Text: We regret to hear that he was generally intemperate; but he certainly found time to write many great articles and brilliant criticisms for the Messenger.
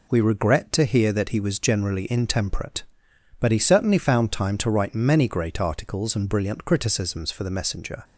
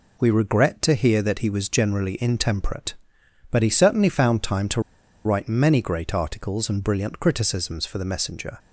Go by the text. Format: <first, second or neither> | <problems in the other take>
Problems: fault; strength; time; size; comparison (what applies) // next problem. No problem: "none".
first | pauses between "to" and "write"; at 4.7 s; 0.45 s long